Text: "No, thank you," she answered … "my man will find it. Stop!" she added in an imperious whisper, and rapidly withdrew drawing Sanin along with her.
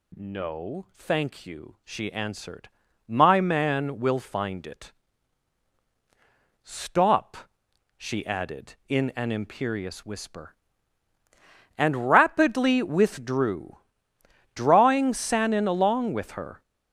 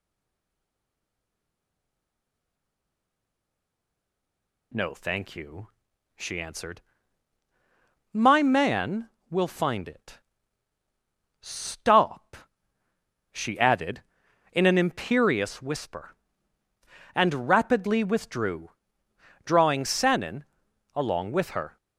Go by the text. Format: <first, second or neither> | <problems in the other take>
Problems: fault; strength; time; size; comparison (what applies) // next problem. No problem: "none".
first | stays silent before the first word; strong; until 4.7 s; 4.7 s long // pauses between "withdrew" and "drawing"; noticeable; at 18.7 s; 0.74 s long; noticeable in the first // pauses between "Sanin" and "along"; noticeable; at 20.4 s; 0.52 s long